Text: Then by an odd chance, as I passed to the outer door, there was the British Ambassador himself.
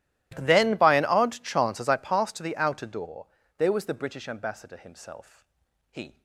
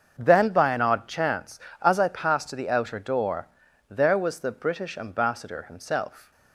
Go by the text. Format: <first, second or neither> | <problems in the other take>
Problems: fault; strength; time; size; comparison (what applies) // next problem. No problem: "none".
second | starts louder than the rest; strong; until 1.3 s; 15.5 dB; also in the second // goes on to say "He"; slight; from 5.9 s on; 0.32 s long